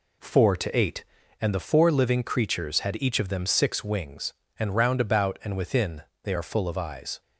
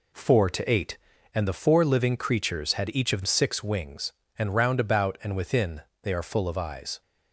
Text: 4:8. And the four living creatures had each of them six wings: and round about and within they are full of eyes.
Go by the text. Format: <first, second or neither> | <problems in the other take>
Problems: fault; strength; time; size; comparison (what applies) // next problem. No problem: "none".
first | skips "them"; at 3.2 s // pauses between "within" and "they"; slight; at 5.8 s; 0.22 s long; slight in the first